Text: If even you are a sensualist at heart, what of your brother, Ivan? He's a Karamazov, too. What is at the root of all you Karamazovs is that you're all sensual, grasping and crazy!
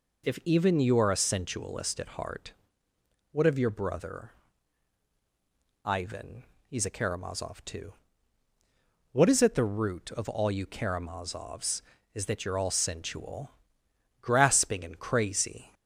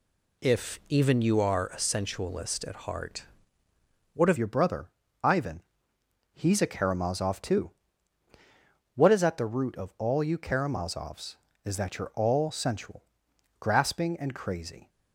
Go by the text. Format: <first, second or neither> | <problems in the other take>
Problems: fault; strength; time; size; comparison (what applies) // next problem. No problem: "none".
first | changes voice at "your"; from 4.3 s on; 10.5 s long